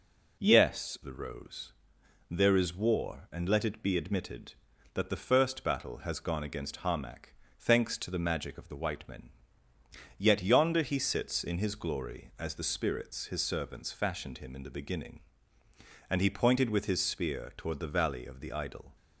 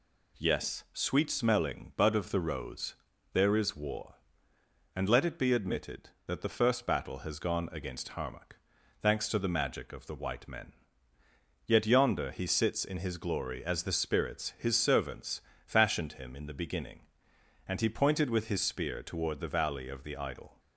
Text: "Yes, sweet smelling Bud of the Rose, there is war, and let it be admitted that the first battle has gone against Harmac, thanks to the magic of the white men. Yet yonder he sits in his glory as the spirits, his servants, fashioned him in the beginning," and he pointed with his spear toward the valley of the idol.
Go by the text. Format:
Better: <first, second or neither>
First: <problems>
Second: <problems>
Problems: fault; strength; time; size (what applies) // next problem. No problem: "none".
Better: second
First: skips "sweet smelling Bud of"; at 1.0 s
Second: none